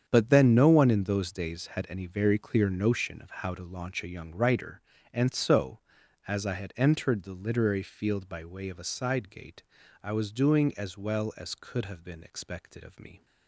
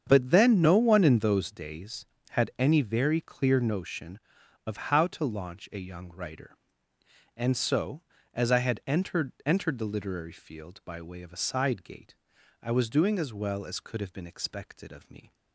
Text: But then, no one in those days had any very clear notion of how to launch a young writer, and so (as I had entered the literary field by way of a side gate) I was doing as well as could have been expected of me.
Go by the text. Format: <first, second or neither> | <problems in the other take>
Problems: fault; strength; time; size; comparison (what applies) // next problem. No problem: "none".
first | starts louder than the rest; strong; until 1.0 s; 7.5 dB; strong in the first // says "entered" twice; at 9.4 s